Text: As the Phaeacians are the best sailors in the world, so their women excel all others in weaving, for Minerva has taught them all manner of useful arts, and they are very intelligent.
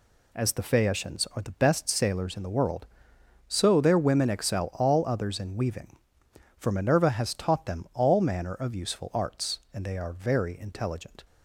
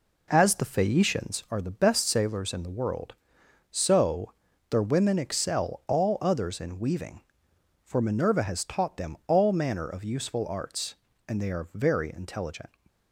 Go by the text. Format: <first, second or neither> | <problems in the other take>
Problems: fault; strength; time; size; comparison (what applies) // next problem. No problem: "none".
first | starts louder than the rest; until 1.5 s; 3.5 dB // pauses between "so" and "their"; at 4.3 s; 0.38 s long